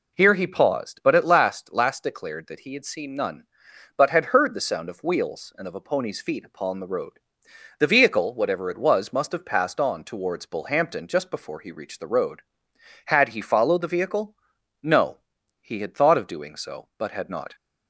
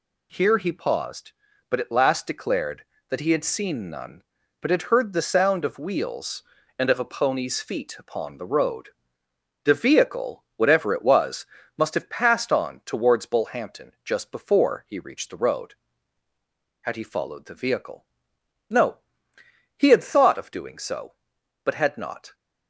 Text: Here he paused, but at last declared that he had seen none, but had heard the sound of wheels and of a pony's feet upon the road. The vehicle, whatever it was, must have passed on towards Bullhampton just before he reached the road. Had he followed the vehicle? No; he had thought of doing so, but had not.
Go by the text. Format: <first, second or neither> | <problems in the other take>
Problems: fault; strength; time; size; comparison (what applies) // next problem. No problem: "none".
second | says "last" twice; at 1.7 s